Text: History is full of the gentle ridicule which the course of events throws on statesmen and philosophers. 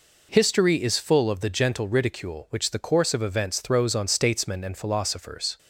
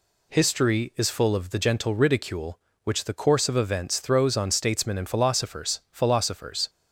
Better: first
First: none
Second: says "philosophers" twice; at 5.9 s

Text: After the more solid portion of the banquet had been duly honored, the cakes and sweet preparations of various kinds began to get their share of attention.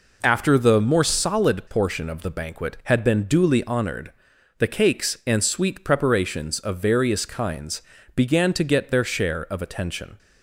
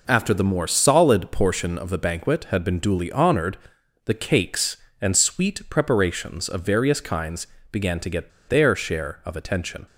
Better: first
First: pauses between "kinds" and "began"; slight; at 7.8 s; 0.34 s long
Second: pauses between "kinds" and "began"; slight; at 7.4 s; 0.26 s long // pauses between "get" and "their"; slight; at 8.3 s; 0.19 s long

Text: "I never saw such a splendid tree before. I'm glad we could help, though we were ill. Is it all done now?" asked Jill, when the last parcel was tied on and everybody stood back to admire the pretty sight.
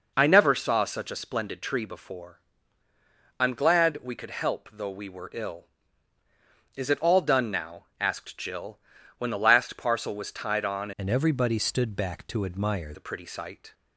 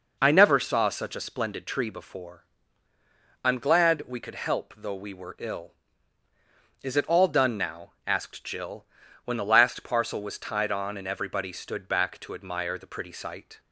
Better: second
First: changes voice from "and" to "admire"; from 10.9 to 12.9 s; 2.0 s long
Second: none

